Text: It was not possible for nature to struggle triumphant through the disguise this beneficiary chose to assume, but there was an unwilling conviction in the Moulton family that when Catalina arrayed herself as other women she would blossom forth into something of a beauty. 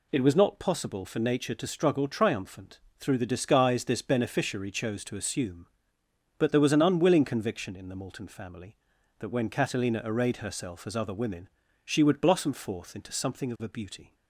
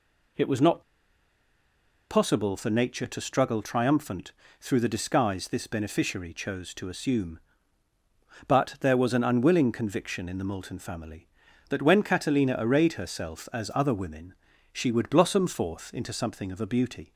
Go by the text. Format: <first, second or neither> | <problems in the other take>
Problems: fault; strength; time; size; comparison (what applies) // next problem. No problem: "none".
first | pauses between "not" and "possible"; strong; at 0.8 s; 1.2 s long // pauses between "triumphant" and "through"; slight; at 4.3 s; 0.28 s long; slight in the first // pauses between "women" and "she"; at 14.3 s; 0.40 s long; also in the first